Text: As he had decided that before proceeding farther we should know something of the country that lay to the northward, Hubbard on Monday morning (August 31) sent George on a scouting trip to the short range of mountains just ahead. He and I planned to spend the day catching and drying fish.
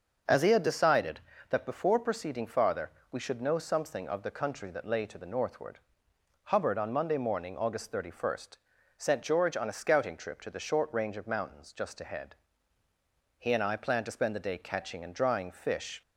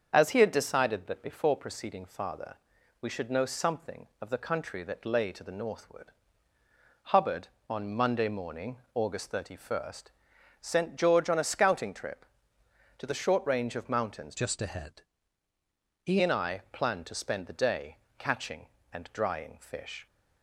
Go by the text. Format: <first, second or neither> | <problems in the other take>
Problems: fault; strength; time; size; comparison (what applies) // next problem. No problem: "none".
first | starts louder than the rest; until 1.1 s; 7 dB; also in the first // pauses between "farther" and "we"; at 2.5 s; 0.44 s long; slight in the first // changes voice from "just" to "He"; from 14.3 to 16.1 s; 1.8 s long // pauses between "day" and "catching"; slight; at 17.9 s; 0.24 s long